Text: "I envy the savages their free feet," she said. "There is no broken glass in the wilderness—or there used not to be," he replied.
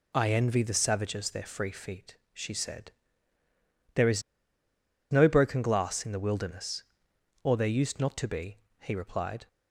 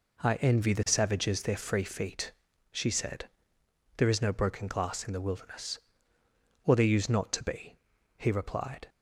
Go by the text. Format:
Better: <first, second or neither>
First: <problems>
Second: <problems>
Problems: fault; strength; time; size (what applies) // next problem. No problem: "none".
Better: second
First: pauses between "is" and "no"; noticeable; at 4.2 s; 0.89 s long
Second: none